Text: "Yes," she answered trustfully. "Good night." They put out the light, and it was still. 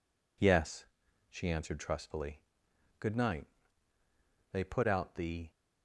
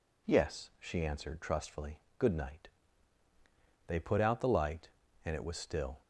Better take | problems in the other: second | stops before "light and it was still"; at 5.5 s

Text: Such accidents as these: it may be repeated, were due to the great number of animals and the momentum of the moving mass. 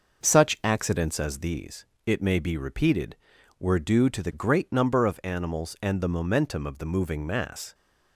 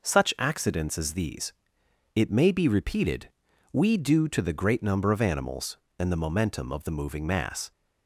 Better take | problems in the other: first | says "we" for "were"; at 3.7 s

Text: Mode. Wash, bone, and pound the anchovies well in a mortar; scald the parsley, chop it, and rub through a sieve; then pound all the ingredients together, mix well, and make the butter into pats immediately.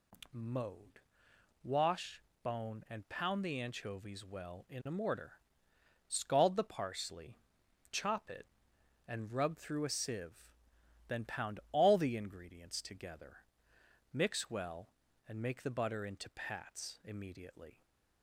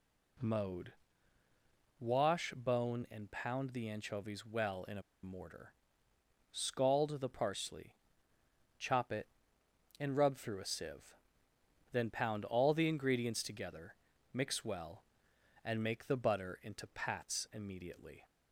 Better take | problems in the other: first | pauses between "a" and "mortar"; slight; at 5.0 s; 0.21 s long

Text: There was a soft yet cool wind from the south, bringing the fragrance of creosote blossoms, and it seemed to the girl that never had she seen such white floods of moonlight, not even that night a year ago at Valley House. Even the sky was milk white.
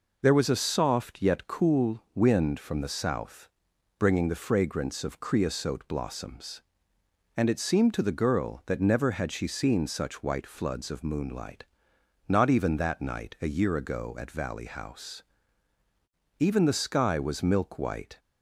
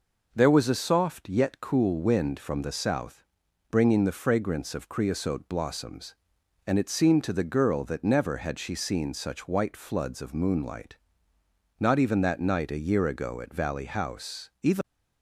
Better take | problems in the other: first | stops before "the sky was milk white"; at 14.8 s

